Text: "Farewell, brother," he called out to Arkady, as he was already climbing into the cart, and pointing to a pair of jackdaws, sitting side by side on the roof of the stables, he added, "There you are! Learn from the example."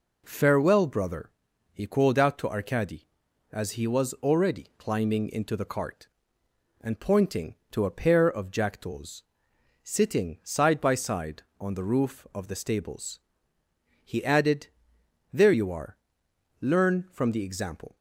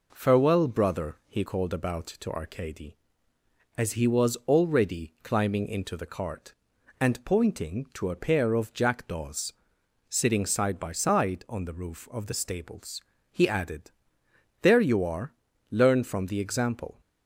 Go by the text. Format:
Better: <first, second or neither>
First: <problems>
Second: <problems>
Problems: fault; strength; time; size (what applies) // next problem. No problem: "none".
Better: first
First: none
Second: says "about" for "out"; at 1.7 s